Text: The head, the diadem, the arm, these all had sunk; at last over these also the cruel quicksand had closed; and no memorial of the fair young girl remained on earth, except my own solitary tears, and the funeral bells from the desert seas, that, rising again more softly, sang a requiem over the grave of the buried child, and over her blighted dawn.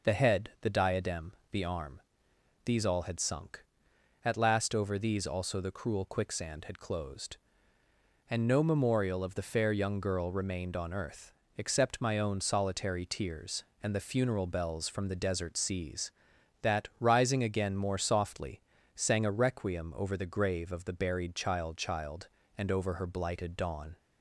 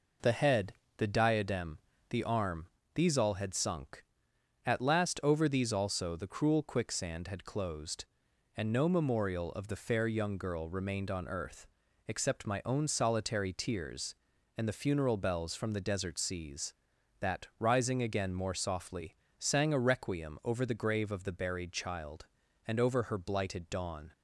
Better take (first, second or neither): second